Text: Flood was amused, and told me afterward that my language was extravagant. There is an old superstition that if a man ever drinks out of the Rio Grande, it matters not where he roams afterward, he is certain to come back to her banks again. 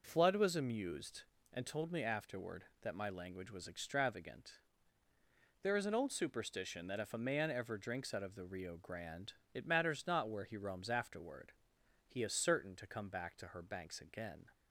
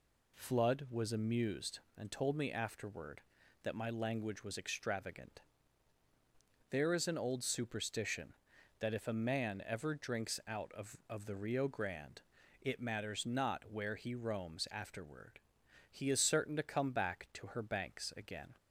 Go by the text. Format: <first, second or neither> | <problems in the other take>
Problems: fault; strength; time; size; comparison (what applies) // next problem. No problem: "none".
first | says "of" twice; at 11.0 s